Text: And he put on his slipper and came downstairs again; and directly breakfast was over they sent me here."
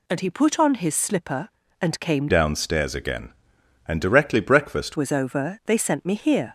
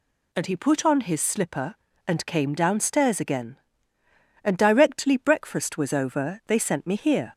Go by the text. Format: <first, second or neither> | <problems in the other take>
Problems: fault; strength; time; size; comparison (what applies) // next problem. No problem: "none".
second | changes voice from "downstairs" to "breakfast"; from 2.2 to 4.9 s; 2.7 s long